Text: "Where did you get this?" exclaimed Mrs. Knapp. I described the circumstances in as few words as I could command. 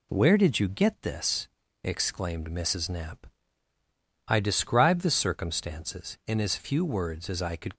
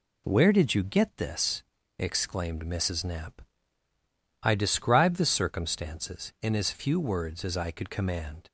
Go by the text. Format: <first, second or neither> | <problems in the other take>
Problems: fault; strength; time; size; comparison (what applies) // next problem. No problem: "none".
second | stops before "command"; at 7.7 s